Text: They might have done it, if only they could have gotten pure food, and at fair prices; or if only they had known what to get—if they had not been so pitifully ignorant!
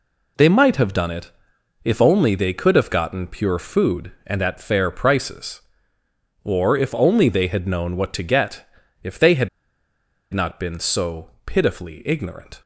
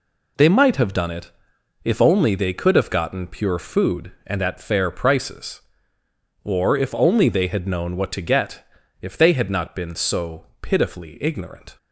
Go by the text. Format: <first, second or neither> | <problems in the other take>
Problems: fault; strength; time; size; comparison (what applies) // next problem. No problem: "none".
second | pauses between "had" and "not"; noticeable; at 9.4 s; 0.84 s long // pauses between "so" and "pitifully"; slight; at 11.2 s; 0.16 s long; slight in the second